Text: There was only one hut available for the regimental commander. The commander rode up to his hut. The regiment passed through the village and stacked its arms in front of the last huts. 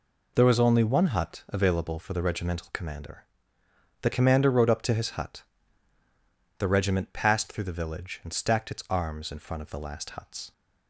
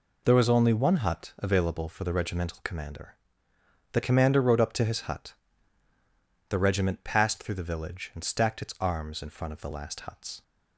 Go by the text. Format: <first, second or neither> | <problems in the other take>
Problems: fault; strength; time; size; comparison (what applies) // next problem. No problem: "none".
neither | none